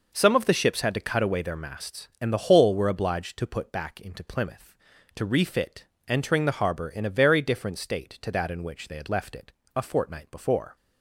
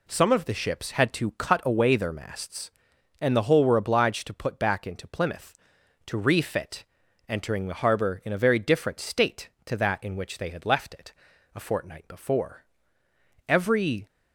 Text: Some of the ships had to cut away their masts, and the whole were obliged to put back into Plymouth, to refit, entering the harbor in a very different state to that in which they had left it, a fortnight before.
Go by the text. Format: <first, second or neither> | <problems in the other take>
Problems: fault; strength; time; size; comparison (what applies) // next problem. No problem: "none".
first | goes on to say "Every"; from 13.4 s on; 0.60 s long